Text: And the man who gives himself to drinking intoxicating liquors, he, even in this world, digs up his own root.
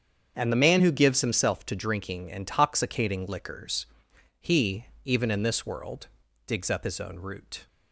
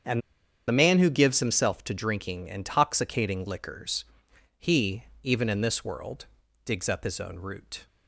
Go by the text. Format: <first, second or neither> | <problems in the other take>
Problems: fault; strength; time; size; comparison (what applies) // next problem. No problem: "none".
first | starts louder than the rest; strong; until 1.5 s; 7.5 dB; strong in the first // pauses between "And" and "the"; noticeable; at 0.2 s; 0.47 s long